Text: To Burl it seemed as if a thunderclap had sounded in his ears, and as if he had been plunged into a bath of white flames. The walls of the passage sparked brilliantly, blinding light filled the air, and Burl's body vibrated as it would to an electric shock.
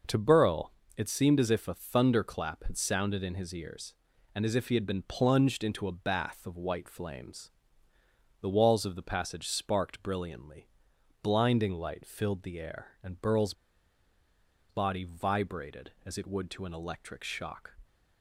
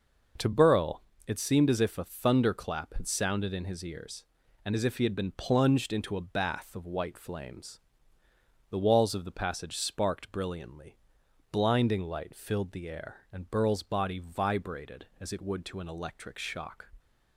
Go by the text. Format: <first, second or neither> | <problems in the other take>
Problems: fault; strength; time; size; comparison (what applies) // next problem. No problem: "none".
second | pauses between "Burl" and "it"; slight; at 0.7 s; 0.24 s long; slight in the second // pauses between "Burl's" and "body"; at 13.5 s; 1.1 s long